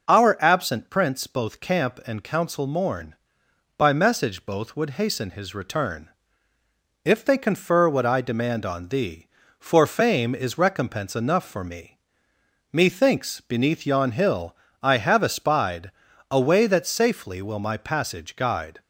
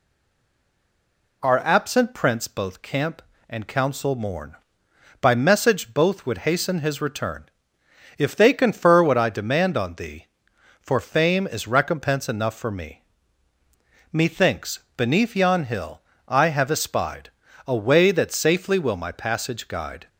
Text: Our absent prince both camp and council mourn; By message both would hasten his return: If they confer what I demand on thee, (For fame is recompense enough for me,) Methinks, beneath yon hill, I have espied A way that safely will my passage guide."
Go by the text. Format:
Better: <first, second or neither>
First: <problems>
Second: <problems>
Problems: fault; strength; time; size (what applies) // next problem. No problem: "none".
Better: first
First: pauses between "espied" and "A"; slight; at 15.9 s; 0.36 s long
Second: stays silent before the first word; noticeable; until 1.4 s; 1.4 s long // pauses between "espied" and "A"; slight; at 17.2 s; 0.36 s long